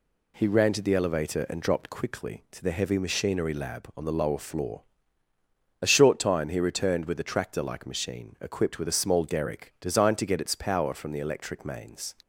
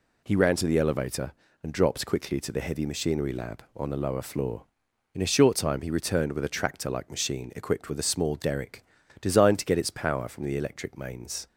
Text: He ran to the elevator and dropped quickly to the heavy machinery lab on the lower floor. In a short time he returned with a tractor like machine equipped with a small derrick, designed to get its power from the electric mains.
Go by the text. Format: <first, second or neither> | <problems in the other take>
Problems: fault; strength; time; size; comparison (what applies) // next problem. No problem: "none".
second | skips "In"; at 5.3 s